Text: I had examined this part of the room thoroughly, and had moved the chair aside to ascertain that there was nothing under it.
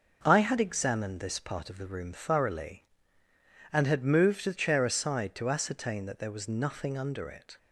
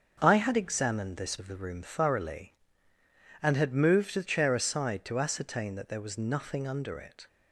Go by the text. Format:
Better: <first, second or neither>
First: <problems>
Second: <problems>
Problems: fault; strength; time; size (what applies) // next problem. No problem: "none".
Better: first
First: none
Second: starts louder than the rest; until 1.2 s; 6.5 dB // skips "part"; at 1.3 s